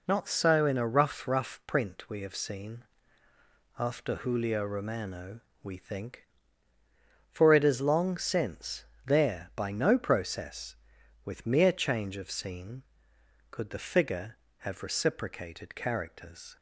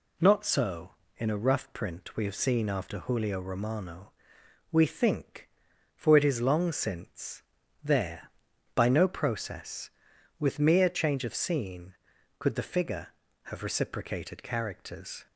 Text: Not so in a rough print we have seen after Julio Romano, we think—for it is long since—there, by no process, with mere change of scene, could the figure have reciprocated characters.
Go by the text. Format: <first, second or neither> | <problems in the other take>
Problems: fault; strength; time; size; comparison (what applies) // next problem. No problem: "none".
second | says "rough" twice; at 1.2 s // pauses between "seen" and "after"; noticeable; at 2.8 s; 0.94 s long